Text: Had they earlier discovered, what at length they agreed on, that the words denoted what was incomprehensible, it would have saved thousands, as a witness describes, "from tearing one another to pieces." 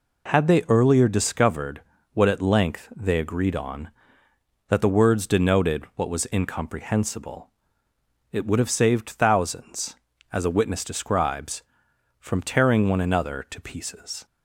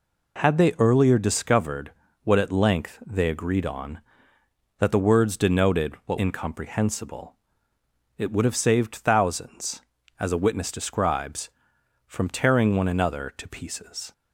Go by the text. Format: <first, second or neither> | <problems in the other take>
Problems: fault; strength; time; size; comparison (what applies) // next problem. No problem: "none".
first | skips "was"; at 6.1 s